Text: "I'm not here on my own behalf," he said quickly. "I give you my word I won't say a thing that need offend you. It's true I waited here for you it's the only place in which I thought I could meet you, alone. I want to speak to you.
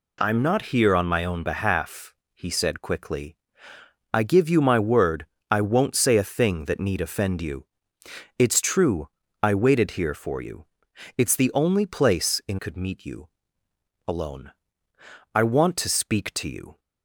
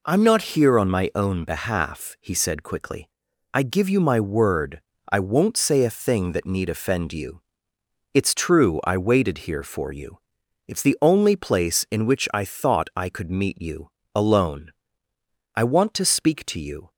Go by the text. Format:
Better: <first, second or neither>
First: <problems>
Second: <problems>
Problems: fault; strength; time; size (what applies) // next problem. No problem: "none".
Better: second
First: pauses between "word" and "I"; slight; at 5.2 s; 0.24 s long // pauses between "true" and "I"; slight; at 9.0 s; 0.34 s long // pauses between "you" and "it's"; noticeable; at 10.6 s; 0.52 s long // skips "which I thought I"; at 12.5 s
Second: pauses between "word" and "I"; slight; at 4.8 s; 0.28 s long // pauses between "you" and "it's"; noticeable; at 10.1 s; 0.48 s long